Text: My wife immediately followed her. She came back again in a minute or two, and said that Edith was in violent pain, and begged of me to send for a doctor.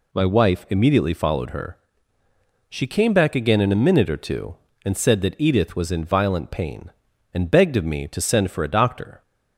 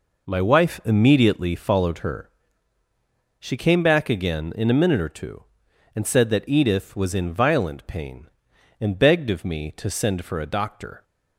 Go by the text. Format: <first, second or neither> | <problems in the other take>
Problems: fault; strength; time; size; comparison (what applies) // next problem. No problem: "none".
neither | none